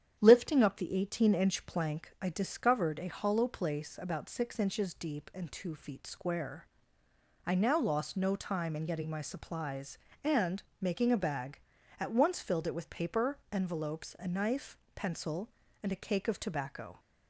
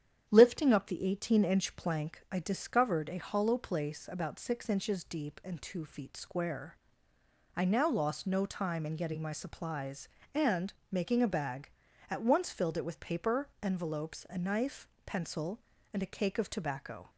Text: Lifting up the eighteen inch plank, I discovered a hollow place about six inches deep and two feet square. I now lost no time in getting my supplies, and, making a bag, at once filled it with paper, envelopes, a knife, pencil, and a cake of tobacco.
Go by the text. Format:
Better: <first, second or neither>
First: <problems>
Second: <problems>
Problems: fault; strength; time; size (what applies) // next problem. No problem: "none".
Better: neither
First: starts louder than the rest; strong; until 1.2 s; 9.5 dB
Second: starts louder than the rest; strong; until 1.3 s; 9.5 dB